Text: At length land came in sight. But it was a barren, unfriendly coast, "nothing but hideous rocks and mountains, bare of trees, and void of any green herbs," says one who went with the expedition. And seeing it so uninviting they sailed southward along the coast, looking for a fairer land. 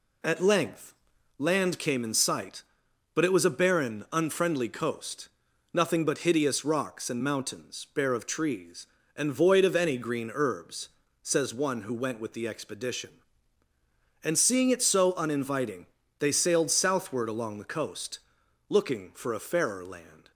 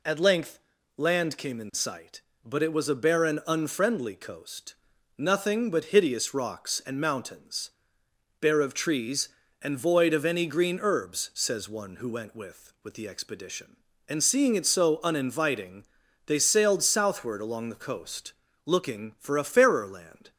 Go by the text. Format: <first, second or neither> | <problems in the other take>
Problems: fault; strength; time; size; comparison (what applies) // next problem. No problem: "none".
first | pauses between "length" and "land"; slight; at 0.5 s; 0.36 s long; also in the first // says "with" twice; at 12.8 s // pauses between "uninviting" and "they"; at 15.8 s; 0.40 s long; slight in the first